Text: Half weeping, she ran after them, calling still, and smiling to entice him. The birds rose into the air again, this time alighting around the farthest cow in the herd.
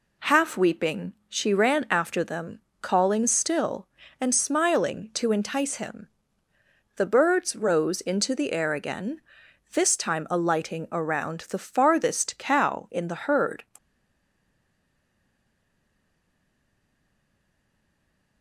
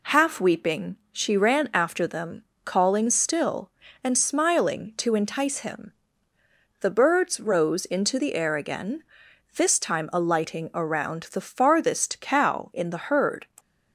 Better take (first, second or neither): second